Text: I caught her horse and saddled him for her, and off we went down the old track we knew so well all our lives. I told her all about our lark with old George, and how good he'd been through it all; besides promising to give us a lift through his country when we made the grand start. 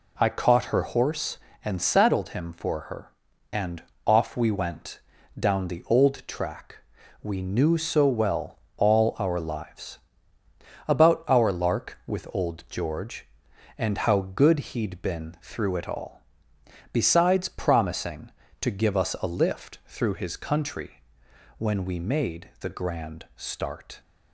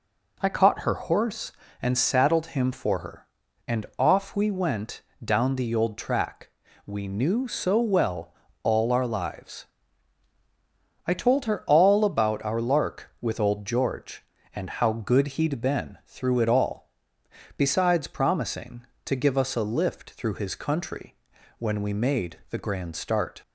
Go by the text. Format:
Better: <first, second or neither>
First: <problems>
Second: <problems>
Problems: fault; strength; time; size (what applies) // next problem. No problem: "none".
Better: second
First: pauses between "and" and "off"; slight; at 3.8 s; 0.24 s long // pauses between "went" and "down"; at 5.0 s; 0.38 s long // pauses between "track" and "we"; at 6.7 s; 0.44 s long // pauses between "well" and "all"; slight; at 8.5 s; 0.20 s long // skips "I told her all"; at 10.4 s // pauses between "country" and "when"; noticeable; at 21.0 s; 0.56 s long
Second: pauses between "went" and "down"; slight; at 5.0 s; 0.22 s long // pauses between "track" and "we"; slight; at 6.4 s; 0.36 s long // pauses between "well" and "all"; slight; at 8.3 s; 0.28 s long // pauses between "country" and "when"; at 21.1 s; 0.42 s long